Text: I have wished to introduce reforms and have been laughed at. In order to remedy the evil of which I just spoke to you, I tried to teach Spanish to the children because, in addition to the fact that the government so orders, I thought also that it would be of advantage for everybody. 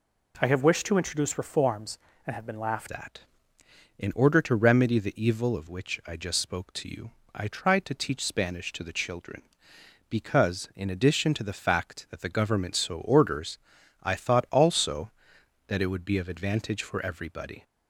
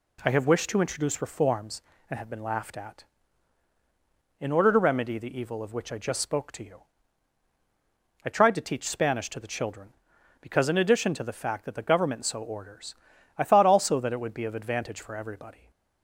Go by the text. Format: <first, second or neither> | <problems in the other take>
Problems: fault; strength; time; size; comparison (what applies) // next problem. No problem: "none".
second | changes voice at "at"; from 2.9 s on; 14.7 s long